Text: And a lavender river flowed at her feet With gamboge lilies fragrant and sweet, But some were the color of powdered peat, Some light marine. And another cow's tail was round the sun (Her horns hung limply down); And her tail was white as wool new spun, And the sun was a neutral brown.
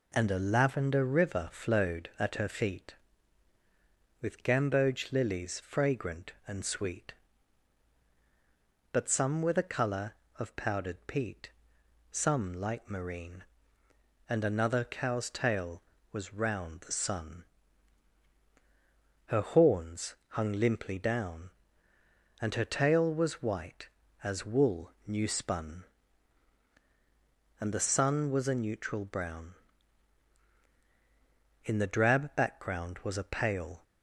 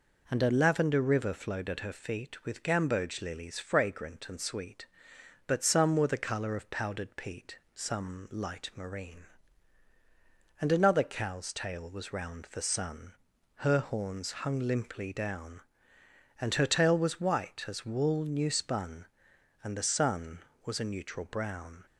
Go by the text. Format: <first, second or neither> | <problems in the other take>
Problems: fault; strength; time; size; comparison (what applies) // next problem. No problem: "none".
second | pauses between "wool" and "new"; slight; at 24.9 s; 0.16 s long // goes on to say "In the drab background was a pale"; strong; from 31.6 s on; 2.1 s long